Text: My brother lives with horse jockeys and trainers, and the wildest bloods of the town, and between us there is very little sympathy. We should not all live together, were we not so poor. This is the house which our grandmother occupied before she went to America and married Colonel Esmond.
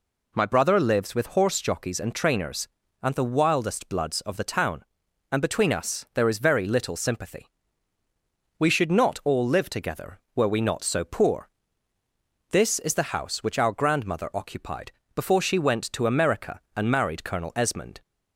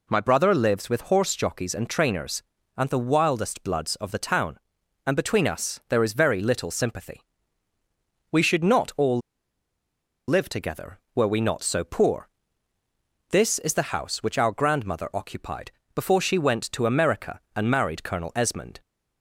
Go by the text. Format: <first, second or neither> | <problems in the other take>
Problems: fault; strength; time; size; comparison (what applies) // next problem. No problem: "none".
first | pauses between "all" and "live"; at 9.1 s; 1.0 s long // pauses between "occupied" and "before"; slight; at 15.7 s; 0.24 s long; slight in the first